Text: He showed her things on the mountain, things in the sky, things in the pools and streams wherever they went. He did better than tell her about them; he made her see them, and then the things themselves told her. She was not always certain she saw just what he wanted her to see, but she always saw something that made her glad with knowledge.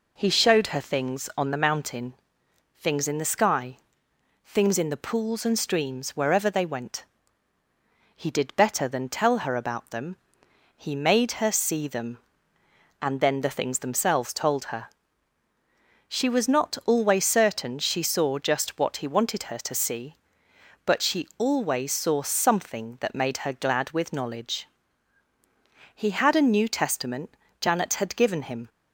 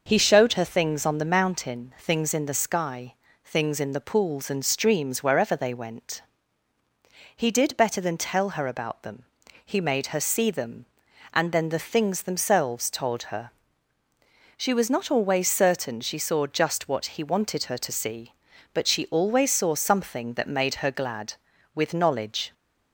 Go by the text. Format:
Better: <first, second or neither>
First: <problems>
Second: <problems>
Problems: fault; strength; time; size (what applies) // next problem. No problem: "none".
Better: second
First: goes on to say "He had a New Testament Janet had given him"; strong; from 25.9 s on; 2.7 s long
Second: none